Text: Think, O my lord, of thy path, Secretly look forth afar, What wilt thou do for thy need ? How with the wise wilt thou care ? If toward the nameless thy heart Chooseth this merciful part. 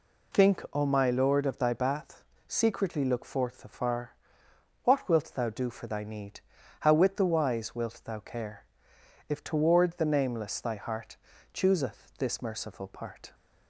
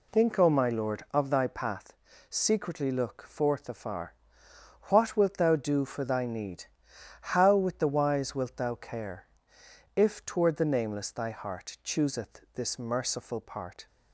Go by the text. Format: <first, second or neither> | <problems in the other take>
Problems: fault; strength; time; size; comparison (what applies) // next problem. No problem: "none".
second | says "bath" for "path"; at 1.7 s // pauses between "heart" and "Chooseth"; slight; at 11.1 s; 0.34 s long